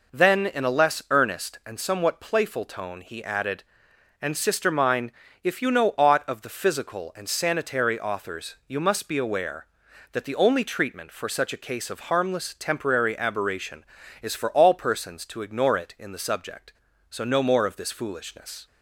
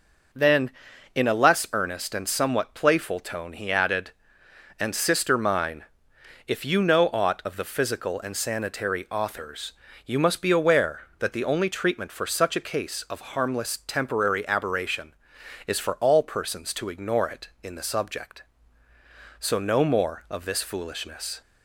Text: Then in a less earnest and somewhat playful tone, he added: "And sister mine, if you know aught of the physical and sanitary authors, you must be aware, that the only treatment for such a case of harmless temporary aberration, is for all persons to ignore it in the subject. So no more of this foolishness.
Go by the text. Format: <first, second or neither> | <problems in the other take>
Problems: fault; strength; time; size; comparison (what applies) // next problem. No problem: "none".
neither | none